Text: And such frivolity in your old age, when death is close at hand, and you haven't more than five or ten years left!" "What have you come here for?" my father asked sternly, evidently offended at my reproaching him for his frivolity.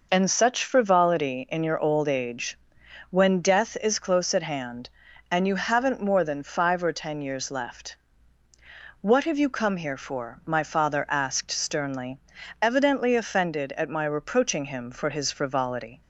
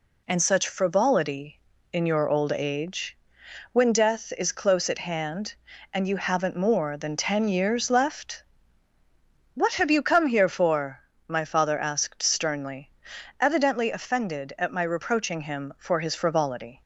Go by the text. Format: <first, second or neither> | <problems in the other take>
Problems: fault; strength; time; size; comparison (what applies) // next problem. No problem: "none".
first | skips "five or"; at 7.1 s